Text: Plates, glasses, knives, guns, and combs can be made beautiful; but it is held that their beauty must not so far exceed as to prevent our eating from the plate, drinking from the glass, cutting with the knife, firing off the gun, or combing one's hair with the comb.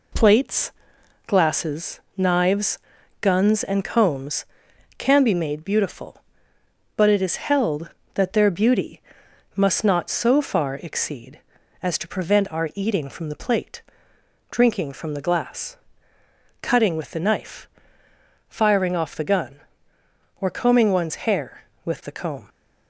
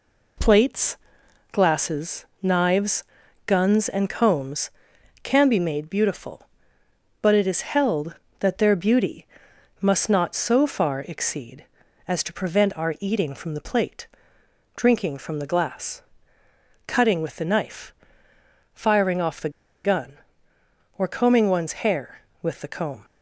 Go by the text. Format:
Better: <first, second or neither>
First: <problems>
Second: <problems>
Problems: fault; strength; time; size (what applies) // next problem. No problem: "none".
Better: first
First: pauses between "beauty" and "must"; noticeable; at 9.0 s; 0.54 s long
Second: pauses between "beauty" and "must"; noticeable; at 9.2 s; 0.54 s long // pauses between "the" and "gun"; slight; at 19.5 s; 0.34 s long